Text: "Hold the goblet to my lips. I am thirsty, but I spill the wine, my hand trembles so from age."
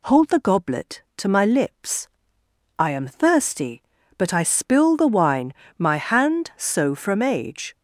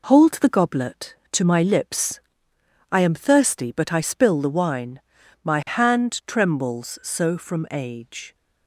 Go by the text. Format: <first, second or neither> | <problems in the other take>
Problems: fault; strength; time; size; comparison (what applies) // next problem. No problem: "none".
second | skips "trembles"; at 6.5 s